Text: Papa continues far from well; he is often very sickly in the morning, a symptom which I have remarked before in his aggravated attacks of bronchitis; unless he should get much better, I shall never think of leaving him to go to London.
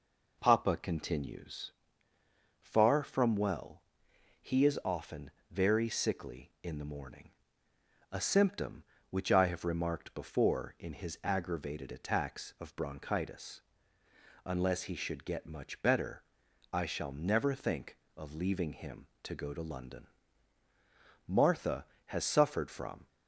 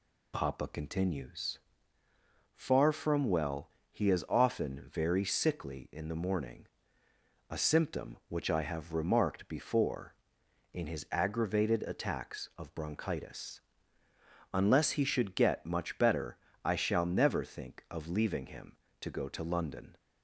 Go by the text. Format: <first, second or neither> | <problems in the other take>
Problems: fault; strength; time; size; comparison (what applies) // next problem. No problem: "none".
second | pauses between "continues" and "far"; noticeable; at 1.7 s; 0.90 s long; noticeable in the second // pauses between "often" and "very"; slight; at 5.3 s; 0.20 s long // goes on to say "Martha has suffered from"; strong; from 21.2 s on; 1.8 s long